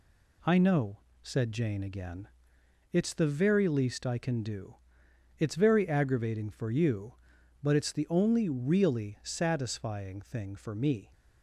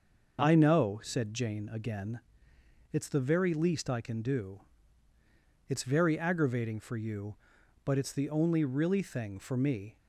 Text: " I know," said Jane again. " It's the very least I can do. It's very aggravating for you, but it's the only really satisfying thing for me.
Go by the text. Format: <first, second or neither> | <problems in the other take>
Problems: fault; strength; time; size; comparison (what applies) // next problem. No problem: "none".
first | starts louder than the rest; until 1.4 s; 6.5 dB // skips "satisfying"; at 9.0 s